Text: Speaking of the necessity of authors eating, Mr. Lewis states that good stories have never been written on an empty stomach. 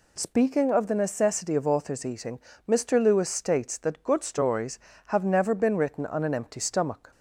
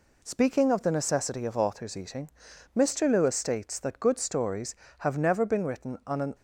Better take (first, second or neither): first